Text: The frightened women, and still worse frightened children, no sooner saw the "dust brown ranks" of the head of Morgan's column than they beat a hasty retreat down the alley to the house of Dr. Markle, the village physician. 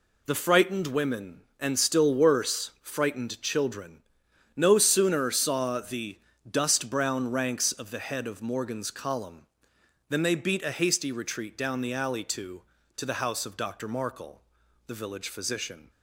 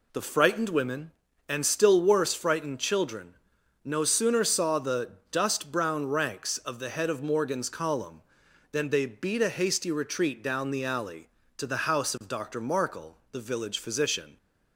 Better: second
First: pauses between "the" and "dust"; slight; at 6.1 s; 0.30 s long // says "to" twice; at 12.9 s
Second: pauses between "the" and "dust"; slight; at 5.1 s; 0.18 s long

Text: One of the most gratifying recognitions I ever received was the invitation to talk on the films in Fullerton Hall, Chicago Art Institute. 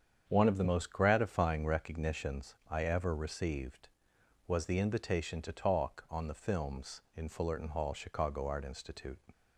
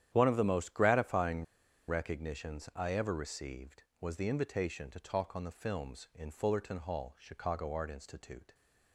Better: first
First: starts louder than the rest; strong; until 1.2 s; 8 dB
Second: starts louder than the rest; strong; until 1.1 s; 10.5 dB // pauses between "gratifying" and "recognitions"; at 1.4 s; 0.44 s long

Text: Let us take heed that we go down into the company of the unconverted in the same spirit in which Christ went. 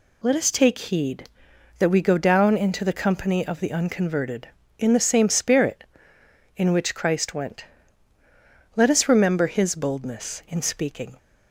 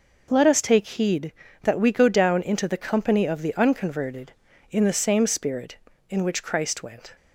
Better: second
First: goes on to say "Let us remember His boldness in speaking"; strong; from 8.7 s on; 2.4 s long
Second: none

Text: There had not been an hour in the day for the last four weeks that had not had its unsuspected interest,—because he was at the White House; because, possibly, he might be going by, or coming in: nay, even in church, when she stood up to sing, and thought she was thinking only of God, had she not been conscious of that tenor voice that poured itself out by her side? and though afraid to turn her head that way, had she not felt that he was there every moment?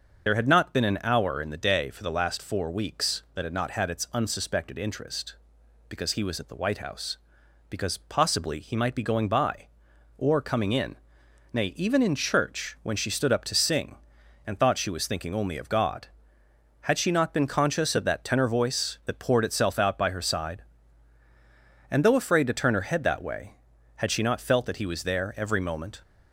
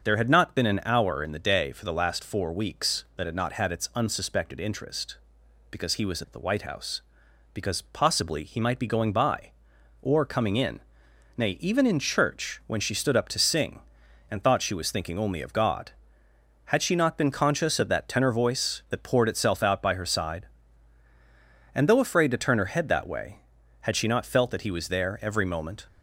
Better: second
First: loses the start of "There"; at 0.2 s; 35 ms // starts louder than the rest; until 1.3 s; 6.5 dB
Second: starts louder than the rest; until 1.1 s; 6.5 dB

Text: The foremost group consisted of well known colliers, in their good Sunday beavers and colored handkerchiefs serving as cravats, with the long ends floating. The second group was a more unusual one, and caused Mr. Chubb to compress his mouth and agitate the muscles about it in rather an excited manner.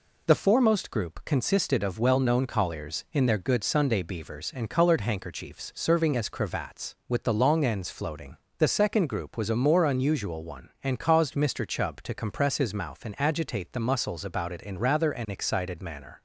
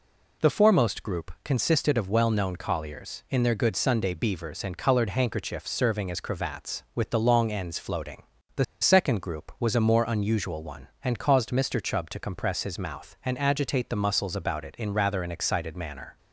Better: first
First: none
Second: pauses between "The" and "second"; slight; at 8.6 s; 0.16 s long

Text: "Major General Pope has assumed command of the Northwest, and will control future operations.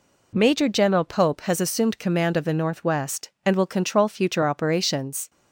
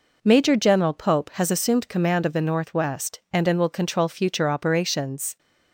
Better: first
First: none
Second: says "and" twice; at 3.4 s

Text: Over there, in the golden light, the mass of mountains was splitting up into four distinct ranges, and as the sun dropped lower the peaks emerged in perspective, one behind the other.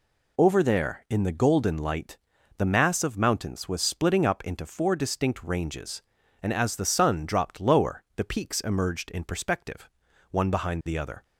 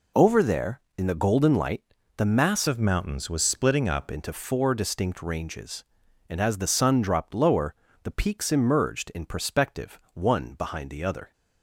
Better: first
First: none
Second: changes voice from "of" to "up"; from 2.6 to 4.0 s; 1.4 s long // pauses between "lower" and "the"; slight; at 7.7 s; 0.30 s long

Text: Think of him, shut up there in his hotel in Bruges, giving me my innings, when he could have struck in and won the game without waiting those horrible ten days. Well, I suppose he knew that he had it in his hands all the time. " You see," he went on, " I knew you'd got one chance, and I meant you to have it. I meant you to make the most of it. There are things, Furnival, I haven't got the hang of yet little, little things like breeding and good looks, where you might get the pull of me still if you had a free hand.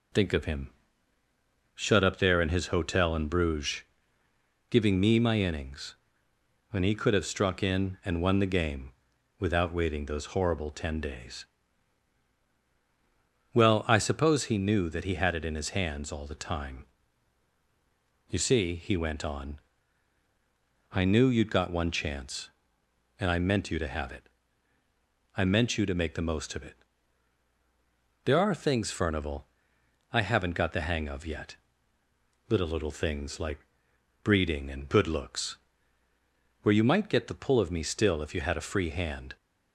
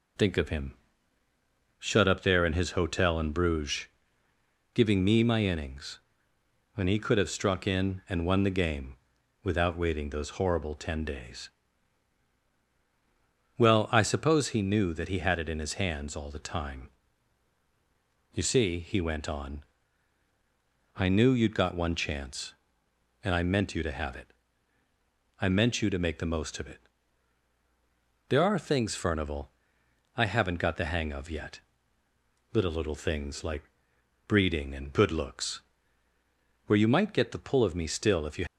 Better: first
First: pauses between "game" and "without"; noticeable; at 8.8 s; 0.50 s long // pauses between "yet" and "little"; noticeable; at 31.5 s; 0.94 s long // pauses between "like" and "breeding"; noticeable; at 33.5 s; 0.64 s long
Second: pauses between "game" and "without"; noticeable; at 8.9 s; 0.50 s long // pauses between "yet" and "little"; noticeable; at 31.6 s; 0.94 s long // pauses between "like" and "breeding"; noticeable; at 33.6 s; 0.64 s long // stops before "had a free hand"; at 38.4 s

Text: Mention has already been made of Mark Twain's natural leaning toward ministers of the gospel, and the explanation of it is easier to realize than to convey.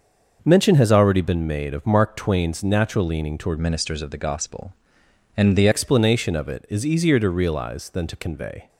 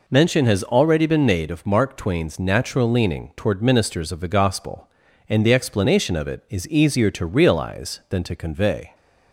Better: second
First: starts louder than the rest; until 1.4 s; 6.5 dB // changes voice from "ministers" to "the"; from 3.5 to 5.6 s; 2.1 s long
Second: none

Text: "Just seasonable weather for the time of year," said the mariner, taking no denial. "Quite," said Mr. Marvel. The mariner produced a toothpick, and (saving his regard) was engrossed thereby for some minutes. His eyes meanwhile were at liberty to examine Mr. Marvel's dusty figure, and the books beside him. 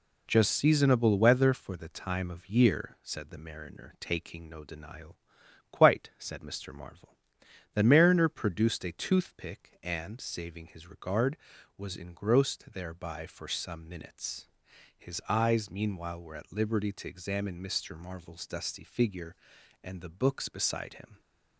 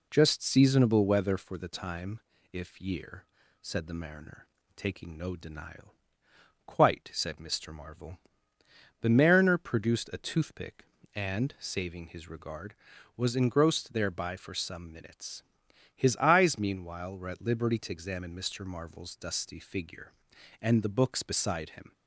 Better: first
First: none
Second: says "if" for "of"; at 2.5 s

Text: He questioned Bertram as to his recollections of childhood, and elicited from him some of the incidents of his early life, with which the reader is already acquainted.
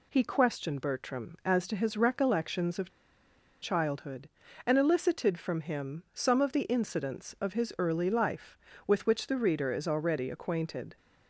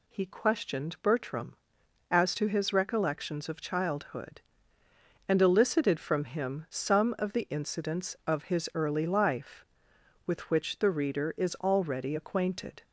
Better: second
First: pauses between "of" and "childhood"; noticeable; at 2.8 s; 0.72 s long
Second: none

